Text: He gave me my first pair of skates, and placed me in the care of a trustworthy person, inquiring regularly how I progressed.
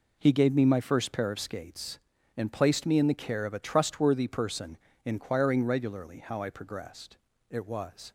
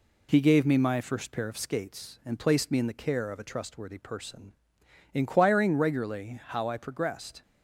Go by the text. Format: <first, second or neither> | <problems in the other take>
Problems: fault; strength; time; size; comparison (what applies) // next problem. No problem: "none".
second | goes on to say "It was"; noticeable; from 7.4 s on; 0.62 s long